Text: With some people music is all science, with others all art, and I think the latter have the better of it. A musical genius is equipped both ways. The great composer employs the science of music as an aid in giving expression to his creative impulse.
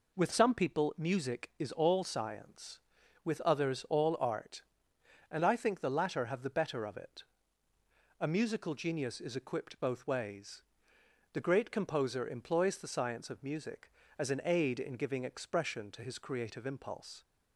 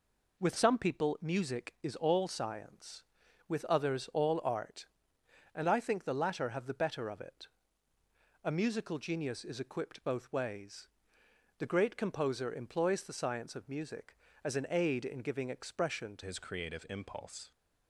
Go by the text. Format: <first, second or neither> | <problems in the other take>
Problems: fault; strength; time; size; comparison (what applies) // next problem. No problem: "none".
first | changes voice at "his"; from 16.2 s on; 1.3 s long